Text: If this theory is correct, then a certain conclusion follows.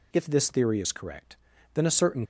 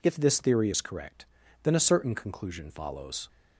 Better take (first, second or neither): second